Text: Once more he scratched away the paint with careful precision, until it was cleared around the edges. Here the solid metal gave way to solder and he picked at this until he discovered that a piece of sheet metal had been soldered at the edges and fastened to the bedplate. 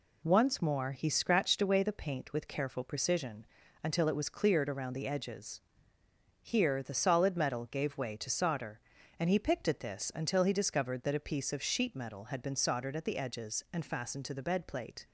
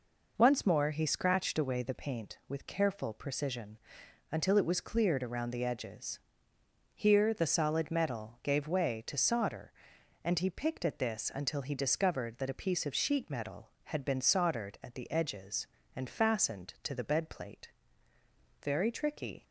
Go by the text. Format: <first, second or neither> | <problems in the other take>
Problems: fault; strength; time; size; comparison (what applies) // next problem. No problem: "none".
first | goes on to say "Very tricky"; noticeable; from 18.6 s on; 0.82 s long